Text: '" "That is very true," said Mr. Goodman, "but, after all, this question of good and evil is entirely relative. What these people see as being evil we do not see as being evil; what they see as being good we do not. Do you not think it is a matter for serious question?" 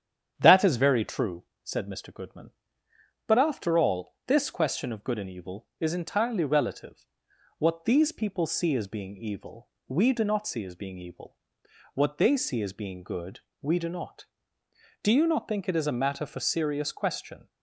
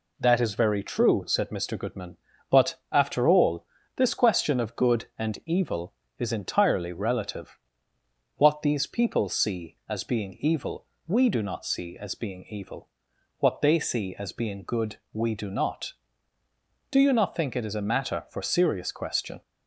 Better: second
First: starts louder than the rest; strong; until 1.6 s; 9 dB // pauses between "evil" and "we"; slight; at 9.7 s; 0.18 s long // pauses between "good" and "we"; slight; at 13.4 s; 0.22 s long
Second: pauses between "evil" and "we"; slight; at 10.8 s; 0.20 s long // pauses between "good" and "we"; slight; at 14.9 s; 0.16 s long

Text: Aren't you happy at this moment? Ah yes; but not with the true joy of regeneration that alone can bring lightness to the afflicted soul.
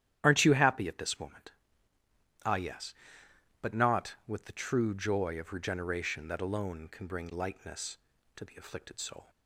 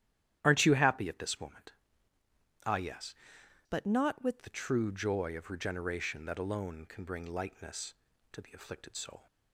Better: first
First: starts louder than the rest; strong; until 1.2 s; 11.5 dB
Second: starts louder than the rest; strong; until 1.4 s; 11.5 dB // changes voice from "but" to "with"; from 3.6 to 4.4 s; 0.8 s long

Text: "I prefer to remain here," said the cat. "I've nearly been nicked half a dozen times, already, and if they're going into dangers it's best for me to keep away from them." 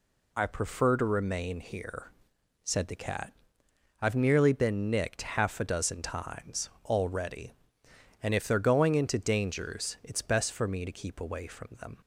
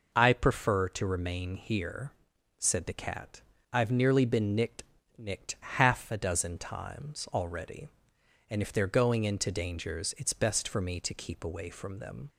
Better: first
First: none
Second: says "nicked" twice; at 5.1 s

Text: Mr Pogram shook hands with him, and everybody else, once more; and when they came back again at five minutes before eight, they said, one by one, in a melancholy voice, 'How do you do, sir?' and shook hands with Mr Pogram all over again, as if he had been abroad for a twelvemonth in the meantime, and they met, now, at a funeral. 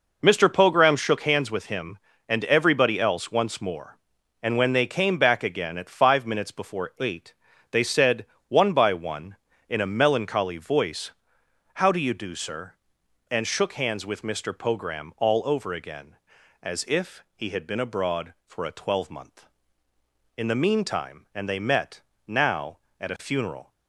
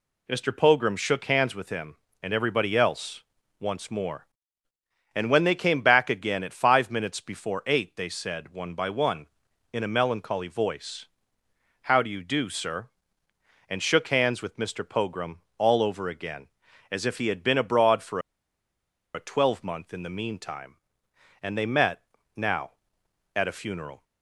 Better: first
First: none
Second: pauses between "Pogram" and "all"; slight; at 15.4 s; 0.16 s long // pauses between "for" and "a"; noticeable; at 18.1 s; 0.94 s long

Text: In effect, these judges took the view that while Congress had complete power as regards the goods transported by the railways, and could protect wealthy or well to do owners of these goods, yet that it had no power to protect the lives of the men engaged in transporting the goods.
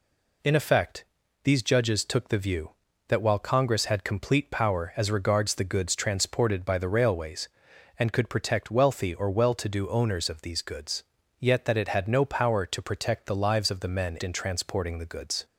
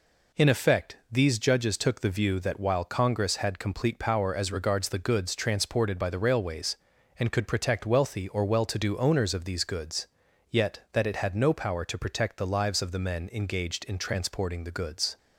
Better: second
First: skips "engaged"; at 14.2 s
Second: none

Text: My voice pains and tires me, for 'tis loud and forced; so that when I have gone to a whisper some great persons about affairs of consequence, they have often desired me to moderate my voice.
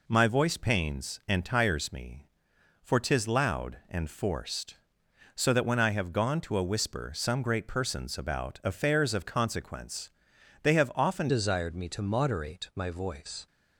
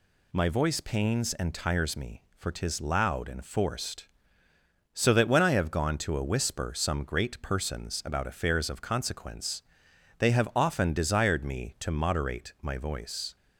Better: second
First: changes voice at "desired"; from 11.2 s on; 2.2 s long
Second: none

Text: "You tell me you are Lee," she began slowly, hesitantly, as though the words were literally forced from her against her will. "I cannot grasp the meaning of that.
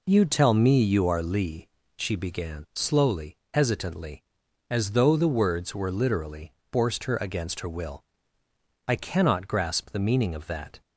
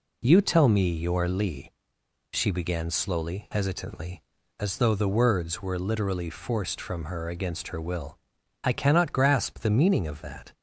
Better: second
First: pauses between "literally" and "forced"; slight; at 6.5 s; 0.22 s long // skips "from"; at 7.0 s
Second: none

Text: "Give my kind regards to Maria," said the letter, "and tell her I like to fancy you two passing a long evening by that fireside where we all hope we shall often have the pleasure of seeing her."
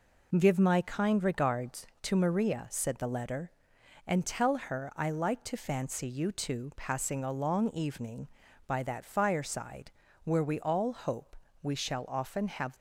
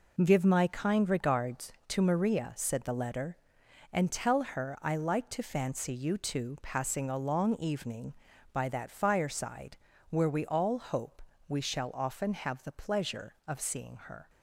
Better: second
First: pauses between "fireside" and "where"; slight; at 9.8 s; 0.36 s long // pauses between "hope" and "we"; slight; at 11.3 s; 0.28 s long // stops before "the pleasure of seeing her"; at 12.7 s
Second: pauses between "fireside" and "where"; slight; at 9.7 s; 0.36 s long // pauses between "hope" and "we"; slight; at 11.2 s; 0.28 s long

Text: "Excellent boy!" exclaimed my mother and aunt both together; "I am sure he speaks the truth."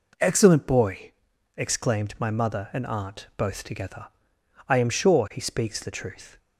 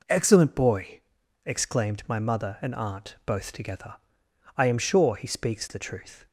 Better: neither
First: none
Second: none

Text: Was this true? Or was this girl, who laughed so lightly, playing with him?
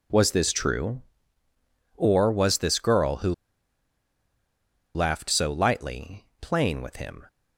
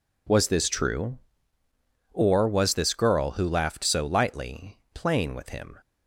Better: second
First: pauses between "who" and "laughed"; strong; at 3.3 s; 1.6 s long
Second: none

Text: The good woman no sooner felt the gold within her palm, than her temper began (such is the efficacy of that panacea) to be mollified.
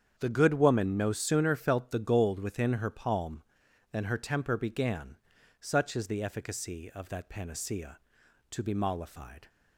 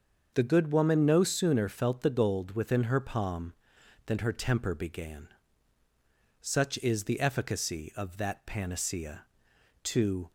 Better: first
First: starts louder than the rest; strong; until 1.1 s; 8 dB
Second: starts louder than the rest; until 1.3 s; 6.5 dB // stops before "be mollified"; at 10.2 s

